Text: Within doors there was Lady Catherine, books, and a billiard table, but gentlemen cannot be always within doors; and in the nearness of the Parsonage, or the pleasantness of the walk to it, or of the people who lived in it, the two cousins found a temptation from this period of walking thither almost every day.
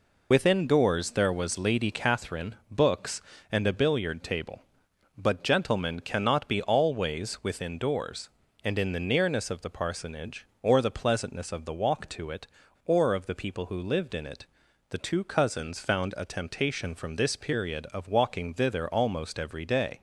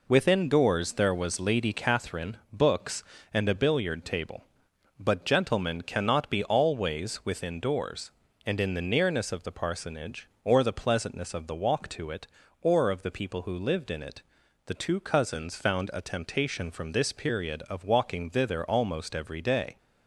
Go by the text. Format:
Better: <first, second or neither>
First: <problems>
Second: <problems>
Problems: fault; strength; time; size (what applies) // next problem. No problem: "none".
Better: second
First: loses the start of "Within"; at 0.3 s; 40 ms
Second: none